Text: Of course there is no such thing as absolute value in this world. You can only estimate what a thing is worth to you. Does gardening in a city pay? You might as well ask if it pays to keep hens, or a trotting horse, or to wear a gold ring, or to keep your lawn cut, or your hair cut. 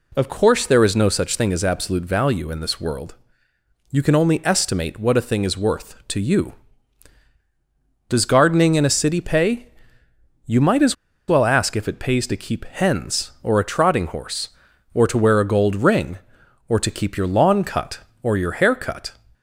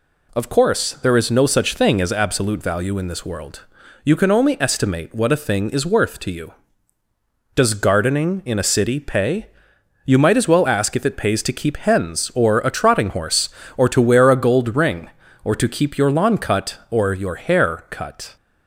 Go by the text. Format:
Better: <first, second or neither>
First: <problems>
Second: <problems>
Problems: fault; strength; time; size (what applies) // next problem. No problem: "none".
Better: second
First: pauses between "as" and "well"; slight; at 10.9 s; 0.33 s long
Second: none